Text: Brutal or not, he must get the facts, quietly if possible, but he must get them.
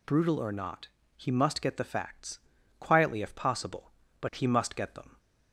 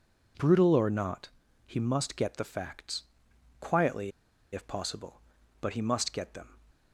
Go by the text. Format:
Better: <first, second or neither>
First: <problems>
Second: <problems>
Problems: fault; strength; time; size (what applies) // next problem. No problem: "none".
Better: first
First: none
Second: pauses between "quietly" and "if"; at 4.1 s; 0.42 s long